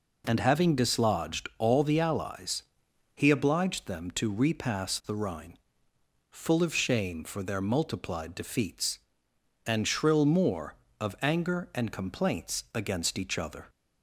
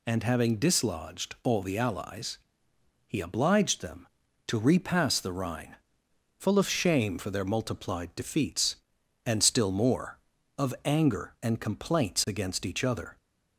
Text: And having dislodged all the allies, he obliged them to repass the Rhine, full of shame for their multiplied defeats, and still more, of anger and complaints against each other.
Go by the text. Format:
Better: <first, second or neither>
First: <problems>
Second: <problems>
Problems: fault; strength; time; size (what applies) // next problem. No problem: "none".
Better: second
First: says "shrill" for "still"; at 9.8 s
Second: none